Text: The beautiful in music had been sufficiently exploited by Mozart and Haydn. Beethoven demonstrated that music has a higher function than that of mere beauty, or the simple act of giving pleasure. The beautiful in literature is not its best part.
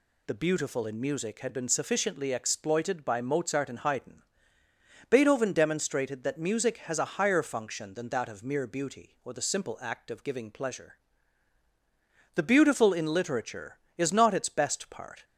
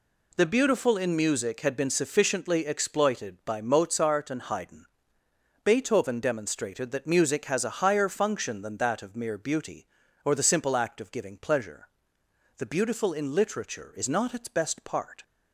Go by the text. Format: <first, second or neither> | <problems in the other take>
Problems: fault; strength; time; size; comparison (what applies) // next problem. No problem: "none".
neither | none